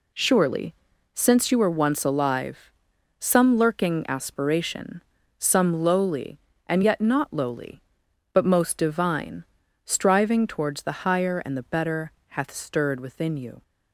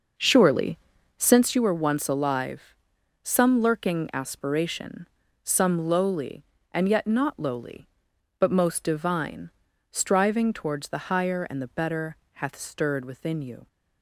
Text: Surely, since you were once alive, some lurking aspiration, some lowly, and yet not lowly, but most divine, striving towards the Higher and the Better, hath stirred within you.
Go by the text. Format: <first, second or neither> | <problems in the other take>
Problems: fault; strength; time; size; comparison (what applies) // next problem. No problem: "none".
first | starts louder than the rest; noticeable; until 1.4 s; 6 dB